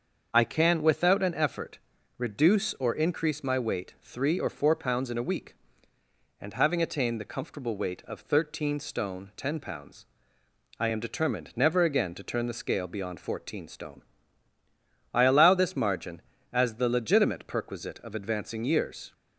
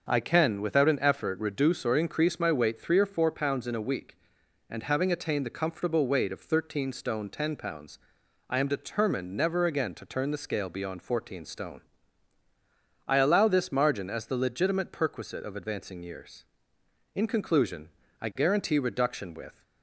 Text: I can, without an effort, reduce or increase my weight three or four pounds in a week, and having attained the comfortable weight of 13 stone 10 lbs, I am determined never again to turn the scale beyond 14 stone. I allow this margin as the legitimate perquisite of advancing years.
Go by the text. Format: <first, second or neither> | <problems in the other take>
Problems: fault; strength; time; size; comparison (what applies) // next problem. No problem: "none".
first | starts louder than the rest; until 1.1 s; 6.5 dB; also in the first // goes on to say "In conclusion I guarantee reduction with"; strong; from 17.1 s on; 2.4 s long